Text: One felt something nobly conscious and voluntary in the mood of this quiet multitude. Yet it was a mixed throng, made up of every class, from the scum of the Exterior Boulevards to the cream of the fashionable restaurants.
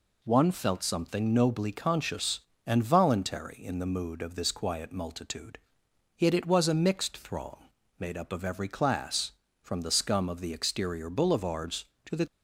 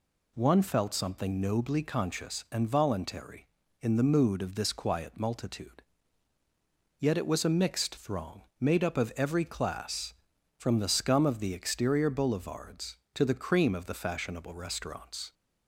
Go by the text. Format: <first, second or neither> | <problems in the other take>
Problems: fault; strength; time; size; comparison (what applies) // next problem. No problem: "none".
second | stops before "cream of the fashionable restaurants"; at 12.2 s